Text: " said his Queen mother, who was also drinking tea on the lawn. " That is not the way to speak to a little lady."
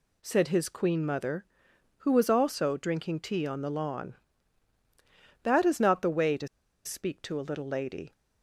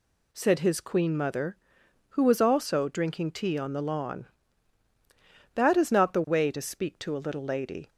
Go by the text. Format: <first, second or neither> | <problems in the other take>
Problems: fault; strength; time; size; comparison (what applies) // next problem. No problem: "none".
second | pauses between "to" and "speak"; at 6.4 s; 0.38 s long